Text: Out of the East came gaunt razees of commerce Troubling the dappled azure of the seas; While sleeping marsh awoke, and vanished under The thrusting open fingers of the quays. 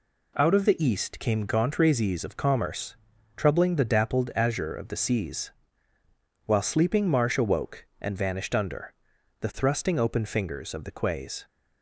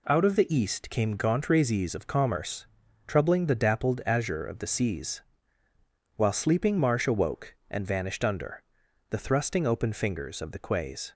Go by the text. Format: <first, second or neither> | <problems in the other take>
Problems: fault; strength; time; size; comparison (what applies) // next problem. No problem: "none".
neither | pauses between "commerce" and "Troubling"; the same in both // pauses between "under" and "The"; noticeable; the same in both